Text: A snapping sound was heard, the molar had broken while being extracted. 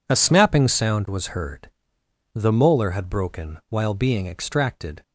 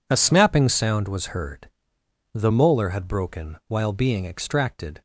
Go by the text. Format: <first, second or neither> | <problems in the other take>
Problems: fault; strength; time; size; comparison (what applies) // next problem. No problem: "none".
neither | none